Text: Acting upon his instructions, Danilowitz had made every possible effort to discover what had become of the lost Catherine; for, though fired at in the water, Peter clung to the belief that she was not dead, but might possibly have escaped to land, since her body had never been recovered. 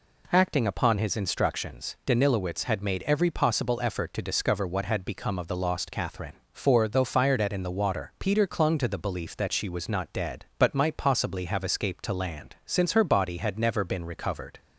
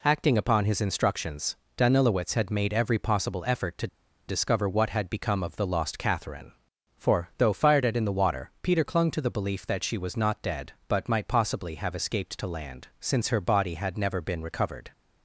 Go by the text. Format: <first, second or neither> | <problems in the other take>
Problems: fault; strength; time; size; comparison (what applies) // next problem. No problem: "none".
first | pauses between "to" and "discover"; at 3.8 s; 0.41 s long